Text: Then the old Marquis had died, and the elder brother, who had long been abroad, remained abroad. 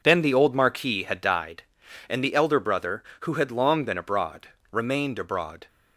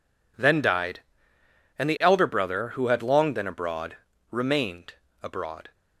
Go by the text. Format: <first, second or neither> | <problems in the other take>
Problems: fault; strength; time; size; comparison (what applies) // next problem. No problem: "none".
first | skips "the old Marquis had"; at 0.6 s // pauses between "remained" and "abroad"; slight; at 4.9 s; 0.30 s long